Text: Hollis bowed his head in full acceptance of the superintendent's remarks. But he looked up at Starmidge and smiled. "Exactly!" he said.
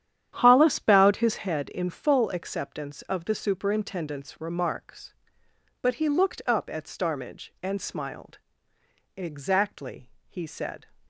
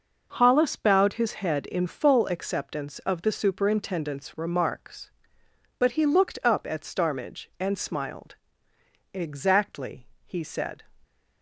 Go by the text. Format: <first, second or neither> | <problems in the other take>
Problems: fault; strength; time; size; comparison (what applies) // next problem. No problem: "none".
second | starts louder than the rest; strong; until 1.5 s; 10 dB